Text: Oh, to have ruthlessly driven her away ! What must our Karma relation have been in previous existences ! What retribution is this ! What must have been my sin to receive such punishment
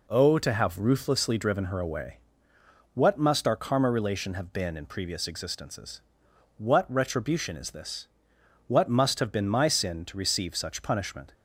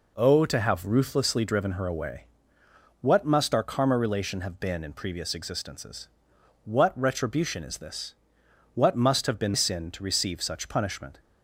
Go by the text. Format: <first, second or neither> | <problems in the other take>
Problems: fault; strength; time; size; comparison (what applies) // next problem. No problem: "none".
first | skips "my"; at 9.5 s